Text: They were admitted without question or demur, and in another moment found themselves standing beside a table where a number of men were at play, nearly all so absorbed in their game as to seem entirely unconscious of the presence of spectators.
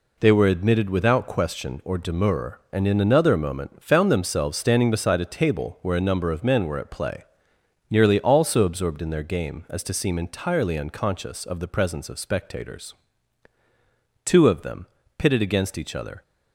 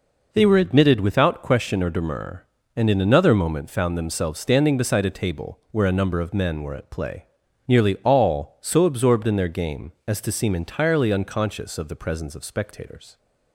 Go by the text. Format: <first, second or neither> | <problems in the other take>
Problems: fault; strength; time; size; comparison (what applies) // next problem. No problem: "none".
second | goes on to say "Two of them pitted against each other"; strong; from 14.2 s on; 1.9 s long